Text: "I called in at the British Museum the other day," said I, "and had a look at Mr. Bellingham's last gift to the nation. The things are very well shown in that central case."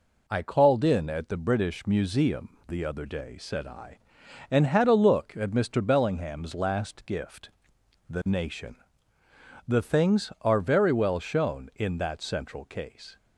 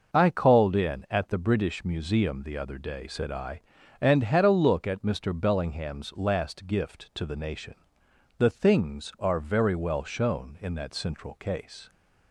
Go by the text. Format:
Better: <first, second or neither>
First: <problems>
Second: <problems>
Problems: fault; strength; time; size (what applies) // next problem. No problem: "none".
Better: second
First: skips "to"; at 7.7 s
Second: none